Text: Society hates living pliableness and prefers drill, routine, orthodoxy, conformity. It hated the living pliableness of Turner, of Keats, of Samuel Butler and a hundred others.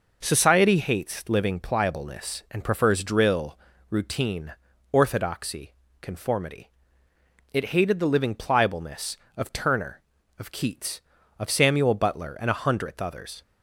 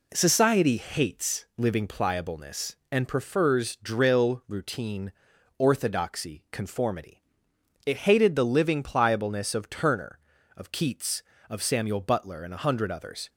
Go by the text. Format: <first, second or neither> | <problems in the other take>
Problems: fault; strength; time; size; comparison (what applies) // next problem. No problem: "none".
second | says "hundredth" for "hundred"; at 12.6 s